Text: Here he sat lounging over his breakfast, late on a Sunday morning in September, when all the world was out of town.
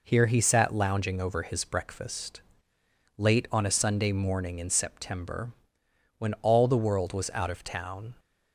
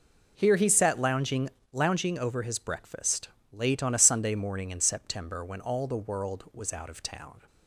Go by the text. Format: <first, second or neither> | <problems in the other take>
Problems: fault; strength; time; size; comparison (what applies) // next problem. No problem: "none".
first | says "lounging" twice; at 1.7 s